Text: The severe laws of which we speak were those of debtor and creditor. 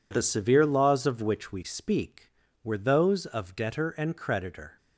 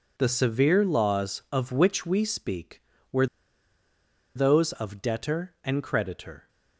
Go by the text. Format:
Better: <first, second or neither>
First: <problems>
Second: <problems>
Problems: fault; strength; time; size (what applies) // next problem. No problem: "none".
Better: first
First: none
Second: pauses between "were" and "those"; at 3.2 s; 1.0 s long